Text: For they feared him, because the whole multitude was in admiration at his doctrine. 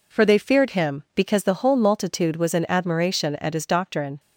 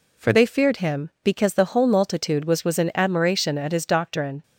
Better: first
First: none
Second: says "was" twice; at 2.6 s

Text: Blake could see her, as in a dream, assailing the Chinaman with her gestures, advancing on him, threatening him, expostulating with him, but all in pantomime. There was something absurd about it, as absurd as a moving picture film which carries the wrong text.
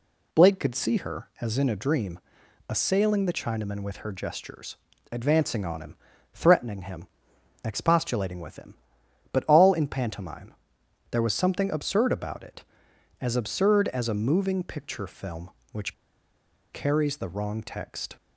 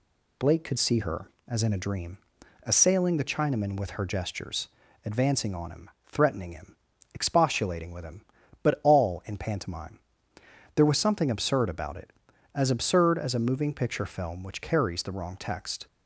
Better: second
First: pauses between "which" and "carries"; noticeable; at 15.9 s; 0.80 s long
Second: none

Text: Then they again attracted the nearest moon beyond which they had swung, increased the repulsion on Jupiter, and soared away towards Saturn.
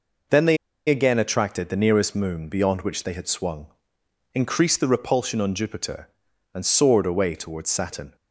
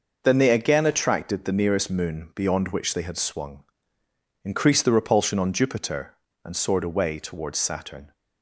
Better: second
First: pauses between "they" and "again"; slight; at 0.5 s; 0.32 s long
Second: none

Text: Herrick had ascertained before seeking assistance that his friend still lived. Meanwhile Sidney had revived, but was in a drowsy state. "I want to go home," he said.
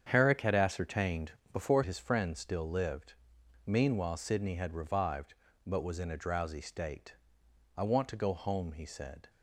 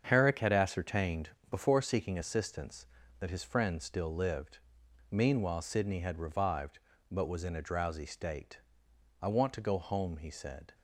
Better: second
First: starts louder than the rest; strong; until 1.1 s; 8 dB // pauses between "ascertained" and "before"; slight; at 1.3 s; 0.18 s long // skips "seeking assistance that"; at 1.8 s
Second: starts louder than the rest; strong; until 1.0 s; 7.5 dB // pauses between "ascertained" and "before"; slight; at 1.3 s; 0.18 s long

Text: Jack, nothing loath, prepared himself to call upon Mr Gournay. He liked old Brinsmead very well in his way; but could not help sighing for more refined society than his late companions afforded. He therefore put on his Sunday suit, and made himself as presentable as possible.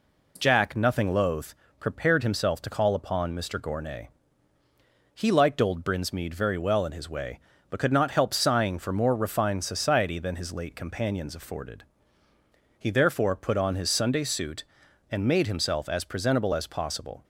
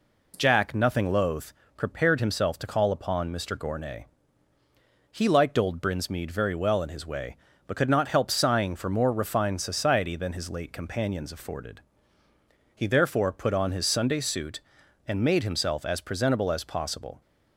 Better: neither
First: none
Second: none

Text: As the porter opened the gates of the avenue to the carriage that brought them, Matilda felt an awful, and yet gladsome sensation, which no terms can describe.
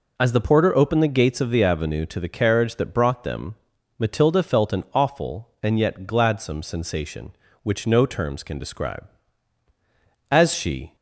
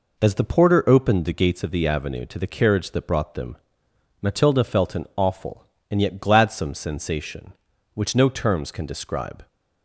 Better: second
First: goes on to say "As she"; noticeable; from 10.2 s on; 0.65 s long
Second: none

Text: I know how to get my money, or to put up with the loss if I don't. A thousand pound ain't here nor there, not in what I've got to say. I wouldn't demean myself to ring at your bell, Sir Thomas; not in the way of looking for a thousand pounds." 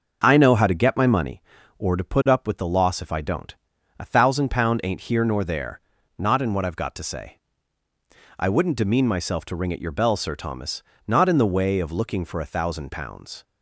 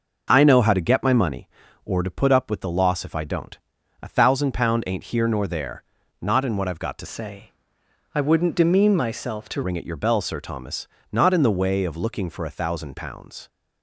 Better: first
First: none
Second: changes voice from "say" to "to"; from 7.0 to 9.6 s; 2.6 s long

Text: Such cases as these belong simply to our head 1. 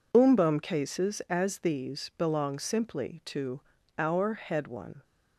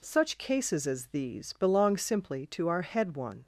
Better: second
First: says "Umbum" for "Such"; at 0.1 s // pauses between "to" and "our"; at 3.6 s; 0.38 s long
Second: none

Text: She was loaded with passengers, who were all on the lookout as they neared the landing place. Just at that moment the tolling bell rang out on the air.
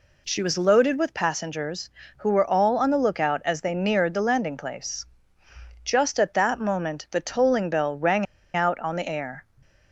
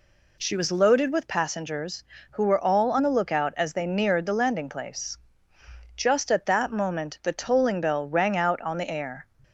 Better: second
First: pauses between "rang" and "out"; slight; at 8.2 s; 0.29 s long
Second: none

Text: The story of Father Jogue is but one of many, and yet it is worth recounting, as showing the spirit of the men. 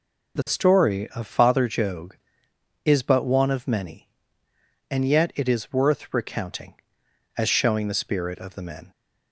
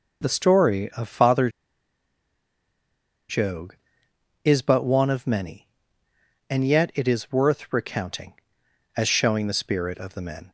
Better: first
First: none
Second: pauses between "Father" and "Jogue"; strong; at 1.4 s; 1.8 s long

